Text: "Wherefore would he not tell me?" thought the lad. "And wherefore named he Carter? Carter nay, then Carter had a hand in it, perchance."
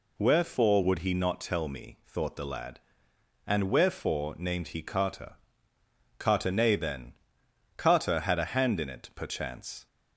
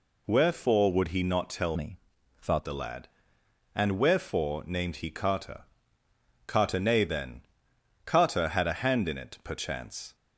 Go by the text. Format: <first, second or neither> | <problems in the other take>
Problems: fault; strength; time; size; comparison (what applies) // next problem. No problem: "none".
first | changes voice from "me" to "thought"; from 1.7 to 2.6 s; 0.9 s long // pauses between "then" and "Carter"; noticeable; at 7.4 s; 0.62 s long; noticeable in the first